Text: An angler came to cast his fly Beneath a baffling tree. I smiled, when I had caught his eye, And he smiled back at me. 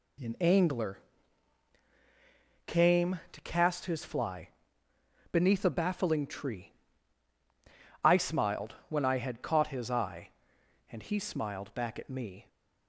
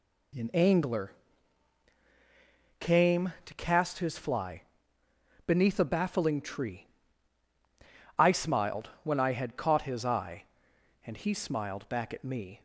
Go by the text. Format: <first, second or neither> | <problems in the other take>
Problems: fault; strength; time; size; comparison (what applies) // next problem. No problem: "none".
neither | pauses between "angler" and "came"; strong; the same in both // pauses between "fly" and "Beneath"; noticeable; the same in both